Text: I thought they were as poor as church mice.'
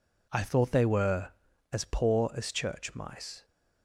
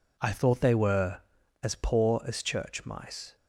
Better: neither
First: none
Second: none

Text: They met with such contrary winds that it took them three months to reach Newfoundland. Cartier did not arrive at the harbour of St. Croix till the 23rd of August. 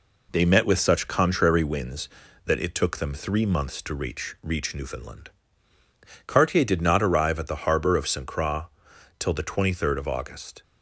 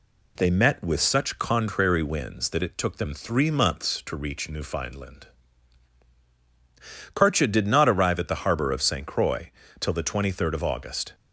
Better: second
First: says "reach" twice; at 4.4 s // pauses between "Croix" and "till"; noticeable; at 8.6 s; 0.54 s long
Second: pauses between "Croix" and "till"; slight; at 9.4 s; 0.32 s long

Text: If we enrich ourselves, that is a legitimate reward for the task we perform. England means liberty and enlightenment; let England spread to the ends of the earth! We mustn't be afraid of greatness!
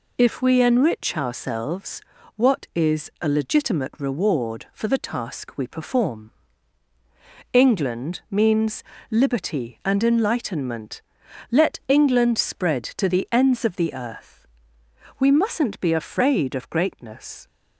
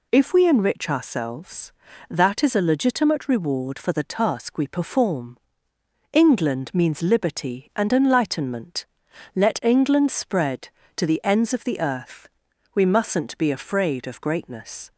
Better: second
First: says "what" for "that"; at 2.3 s // pauses between "means" and "liberty"; slight; at 8.8 s; 0.28 s long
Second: none

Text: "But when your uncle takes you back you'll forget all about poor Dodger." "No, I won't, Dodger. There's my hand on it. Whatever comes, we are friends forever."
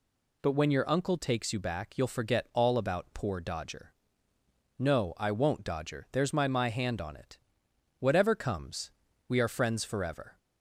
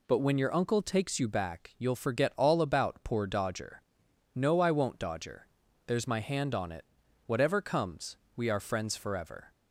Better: second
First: says "my" twice; at 6.4 s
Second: none

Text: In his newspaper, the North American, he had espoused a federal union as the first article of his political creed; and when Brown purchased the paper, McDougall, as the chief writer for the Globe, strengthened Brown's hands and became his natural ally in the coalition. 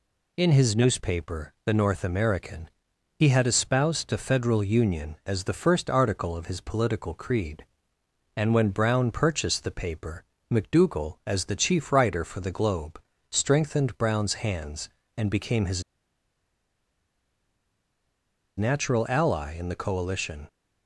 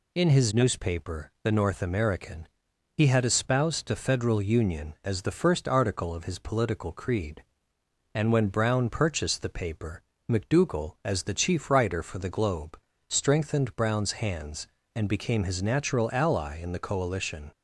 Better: second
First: pauses between "his" and "natural"; strong; at 15.8 s; 2.7 s long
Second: none

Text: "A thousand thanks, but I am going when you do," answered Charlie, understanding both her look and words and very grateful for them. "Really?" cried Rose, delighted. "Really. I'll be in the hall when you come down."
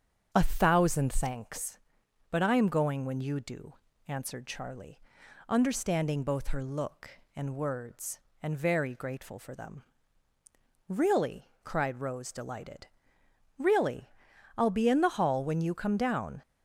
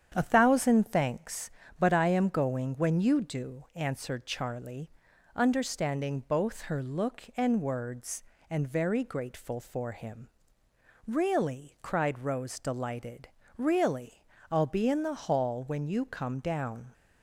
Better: first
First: starts louder than the rest; strong; until 1.3 s; 7.5 dB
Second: starts louder than the rest; strong; until 1.1 s; 8.5 dB // says "him" for "them"; at 9.9 s

